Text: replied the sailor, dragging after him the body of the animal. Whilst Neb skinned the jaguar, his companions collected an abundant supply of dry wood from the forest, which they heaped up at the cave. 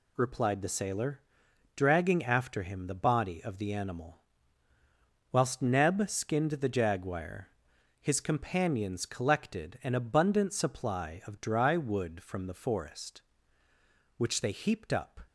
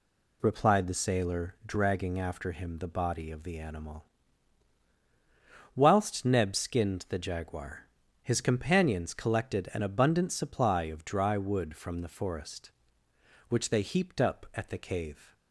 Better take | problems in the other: second | stops before "at the cave"; at 15.2 s

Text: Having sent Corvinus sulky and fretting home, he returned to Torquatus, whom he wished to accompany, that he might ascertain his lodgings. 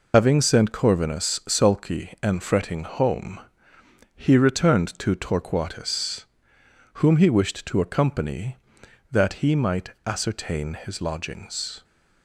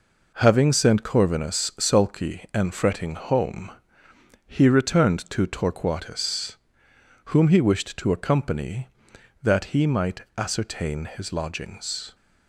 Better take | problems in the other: second | loses the start of "Having"; at 0.1 s; 105 ms

